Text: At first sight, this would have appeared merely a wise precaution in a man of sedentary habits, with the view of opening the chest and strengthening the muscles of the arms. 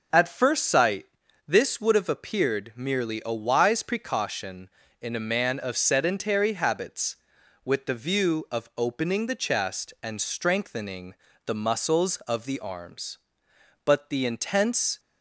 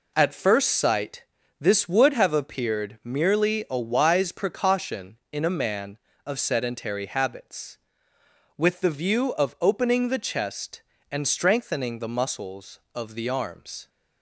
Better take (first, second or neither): second